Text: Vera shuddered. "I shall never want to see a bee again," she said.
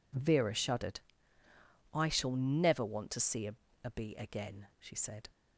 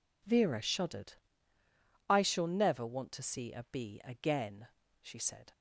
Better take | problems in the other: second | says "a" twice; at 3.8 s

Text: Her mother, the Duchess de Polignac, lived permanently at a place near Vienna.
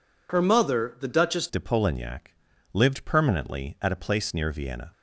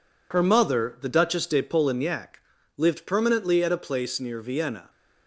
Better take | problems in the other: second | changes voice at "de"; from 1.4 s on; 3.5 s long

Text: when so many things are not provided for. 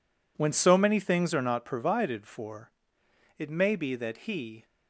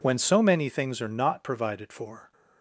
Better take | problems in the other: second | goes on to say "It may be that he"; noticeable; from 3.3 s on; 1.2 s long

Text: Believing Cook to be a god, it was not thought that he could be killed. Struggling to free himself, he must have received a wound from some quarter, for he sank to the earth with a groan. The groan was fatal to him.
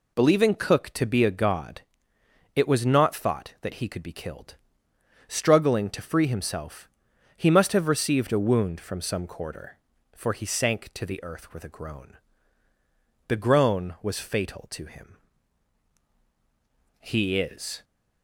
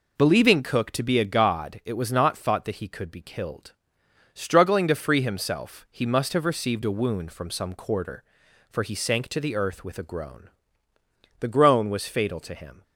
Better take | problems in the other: second | goes on to say "He is"; noticeable; from 16.9 s on; 0.84 s long

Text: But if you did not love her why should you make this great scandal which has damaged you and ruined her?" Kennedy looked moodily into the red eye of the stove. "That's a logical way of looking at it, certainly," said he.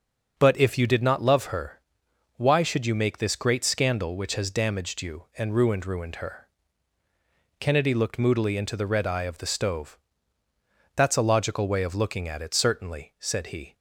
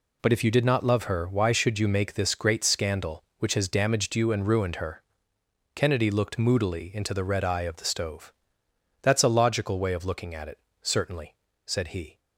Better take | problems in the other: second | starts louder than the rest; until 1.4 s; 6.5 dB // pauses between "her" and "why"; noticeable; at 1.8 s; 0.56 s long // says "ruined" twice; at 5.8 s

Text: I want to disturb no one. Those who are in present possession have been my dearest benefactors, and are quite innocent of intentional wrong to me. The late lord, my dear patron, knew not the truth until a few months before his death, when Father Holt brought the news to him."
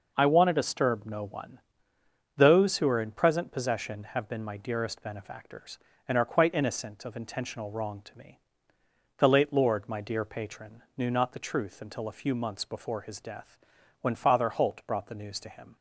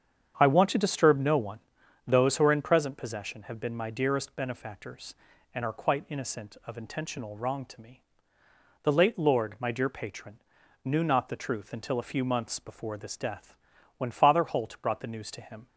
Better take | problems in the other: first | starts louder than the rest; strong; until 1.4 s; 8 dB // says "this" for "his"; at 12.9 s

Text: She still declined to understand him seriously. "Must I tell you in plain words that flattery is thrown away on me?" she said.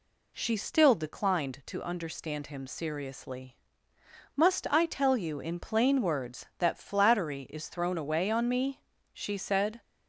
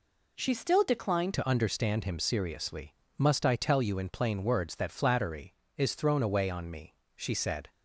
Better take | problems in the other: first | changes voice at "to"; from 1.3 s on; 6.3 s long

